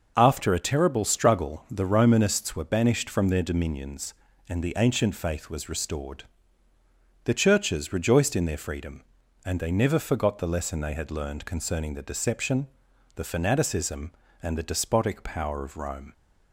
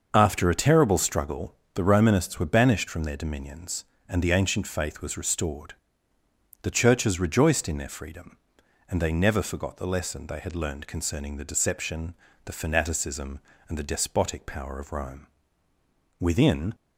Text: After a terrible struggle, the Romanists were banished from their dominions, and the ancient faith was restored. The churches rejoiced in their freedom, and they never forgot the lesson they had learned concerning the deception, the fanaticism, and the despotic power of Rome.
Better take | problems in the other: first | starts louder than the rest; until 1.1 s; 6.5 dB; noticeable in the first // goes on to say "Within"; from 16.1 s on; 0.56 s long

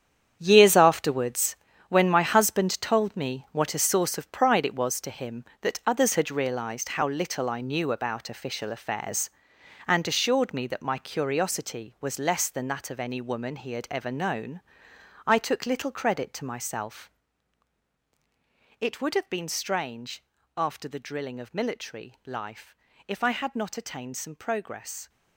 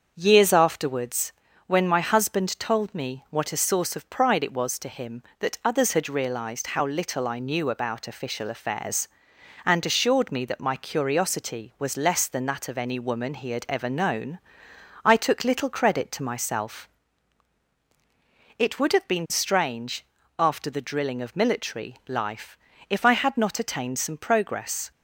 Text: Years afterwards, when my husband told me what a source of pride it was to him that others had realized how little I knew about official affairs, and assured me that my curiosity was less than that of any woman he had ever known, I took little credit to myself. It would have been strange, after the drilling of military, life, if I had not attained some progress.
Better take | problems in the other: second | gets quieter; strong; throughout; 11.5 dB // starts louder than the rest; strong; until 1.4 s; 8.5 dB; also in the second

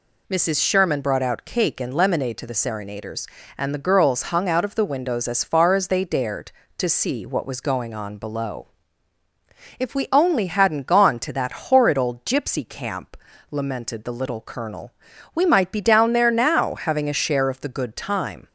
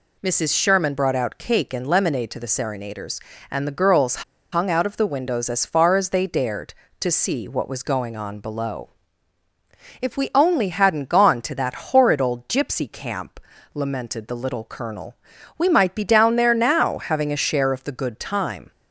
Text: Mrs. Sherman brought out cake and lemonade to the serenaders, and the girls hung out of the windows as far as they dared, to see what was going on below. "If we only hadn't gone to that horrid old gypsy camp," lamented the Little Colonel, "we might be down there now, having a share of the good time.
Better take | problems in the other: first | pauses between "girls" and "hung"; slight; at 4.2 s; 0.30 s long

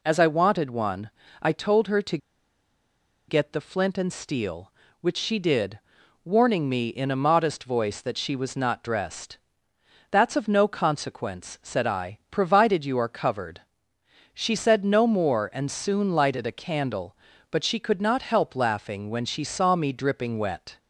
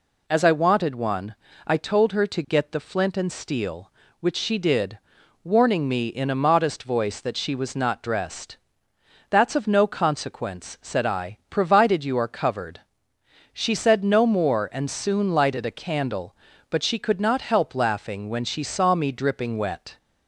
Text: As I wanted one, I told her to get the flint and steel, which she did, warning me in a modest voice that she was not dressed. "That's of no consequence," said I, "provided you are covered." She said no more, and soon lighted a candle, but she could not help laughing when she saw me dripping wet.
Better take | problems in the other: second | pauses between "to" and "get"; at 2.1 s; 1.1 s long

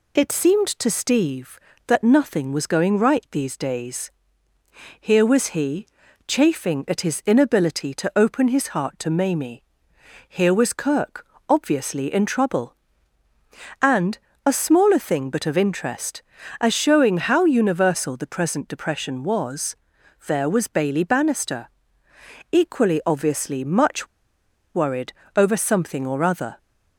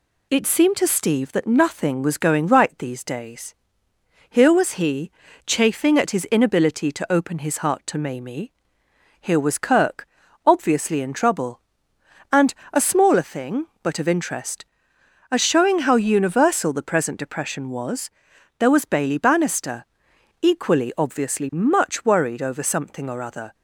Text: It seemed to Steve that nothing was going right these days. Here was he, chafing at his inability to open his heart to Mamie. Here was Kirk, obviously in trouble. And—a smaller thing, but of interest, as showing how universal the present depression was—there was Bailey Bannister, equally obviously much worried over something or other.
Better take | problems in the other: second | pauses between "much" and "worried"; noticeable; at 24.0 s; 0.69 s long // pauses between "worried" and "over"; slight; at 25.1 s; 0.20 s long

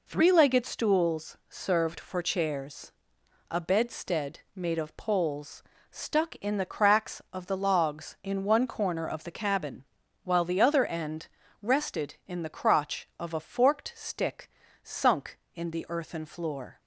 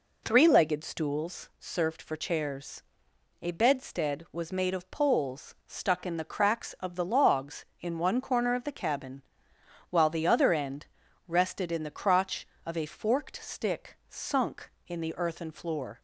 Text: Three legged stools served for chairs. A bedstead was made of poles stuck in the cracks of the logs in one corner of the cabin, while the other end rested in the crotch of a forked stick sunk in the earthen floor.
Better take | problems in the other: second | skips "was"; at 4.4 s // pauses between "poles" and "stuck"; slight; at 5.6 s; 0.30 s long // pauses between "end" and "rested"; slight; at 11.2 s; 0.34 s long; also in the second // pauses between "stick" and "sunk"; slight; at 14.4 s; 0.32 s long

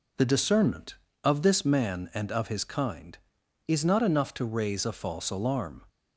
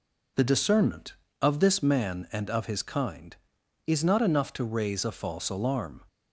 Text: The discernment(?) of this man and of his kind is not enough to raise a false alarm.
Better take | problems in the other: neither | none

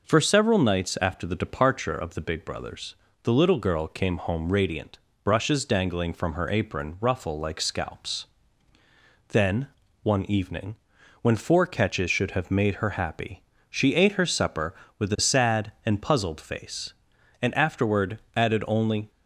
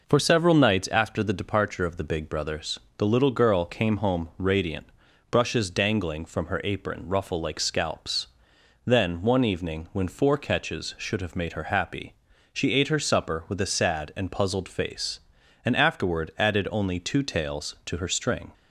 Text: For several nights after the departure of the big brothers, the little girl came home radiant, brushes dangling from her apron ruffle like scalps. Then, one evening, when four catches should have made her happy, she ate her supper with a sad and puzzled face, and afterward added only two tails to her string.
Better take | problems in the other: second | pauses between "afterward" and "added"; slight; at 18.1 s; 0.16 s long // stops before "two tails to her string"; at 19.0 s

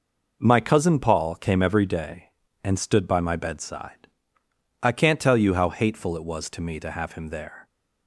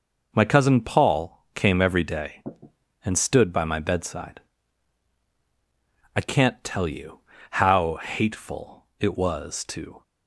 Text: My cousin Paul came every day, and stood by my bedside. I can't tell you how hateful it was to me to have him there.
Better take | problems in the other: first | pauses between "you" and "how"; slight; at 7.1 s; 0.32 s long // stops before "me to have him there"; at 10.0 s

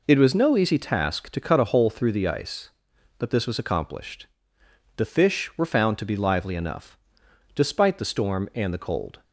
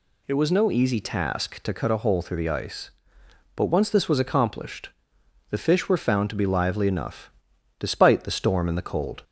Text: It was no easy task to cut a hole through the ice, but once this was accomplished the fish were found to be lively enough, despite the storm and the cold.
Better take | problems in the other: second | skips "once"; at 3.2 s // pauses between "accomplished" and "the"; noticeable; at 4.2 s; 0.70 s long; noticeable in the second

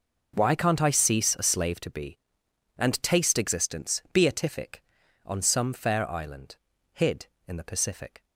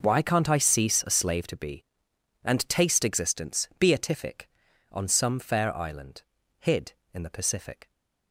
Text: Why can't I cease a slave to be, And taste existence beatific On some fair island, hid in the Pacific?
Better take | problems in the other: neither | none

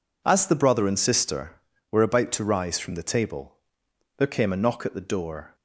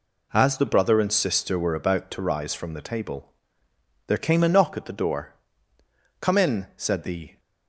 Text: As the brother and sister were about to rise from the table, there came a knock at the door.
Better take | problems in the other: first | goes on to say "Come in said the"; noticeable; from 6.1 s on; 1.2 s long

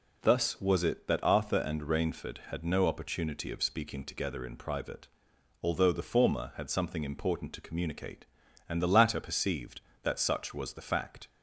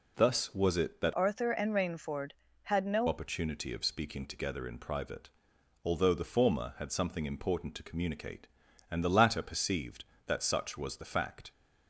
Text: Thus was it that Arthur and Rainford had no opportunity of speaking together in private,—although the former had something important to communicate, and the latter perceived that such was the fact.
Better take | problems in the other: first | changes voice from "Arthur" to "no"; from 1.1 to 3.0 s; 1.9 s long

